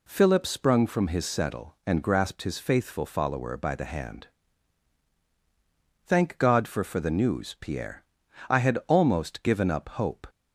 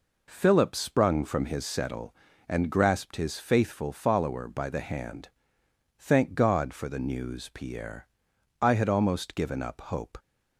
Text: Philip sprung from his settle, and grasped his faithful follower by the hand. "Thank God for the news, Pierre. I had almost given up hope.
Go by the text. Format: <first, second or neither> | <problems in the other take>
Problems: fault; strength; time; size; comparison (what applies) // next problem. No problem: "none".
second | says "for" twice; at 6.8 s